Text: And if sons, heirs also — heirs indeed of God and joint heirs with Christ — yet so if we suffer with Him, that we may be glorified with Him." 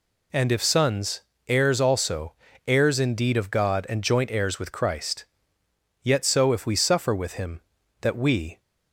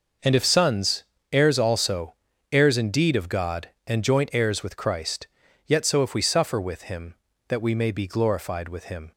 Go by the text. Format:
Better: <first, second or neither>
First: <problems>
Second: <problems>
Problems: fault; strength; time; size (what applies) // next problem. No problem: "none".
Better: second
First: stops before "may be glorified with Him"; at 8.5 s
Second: none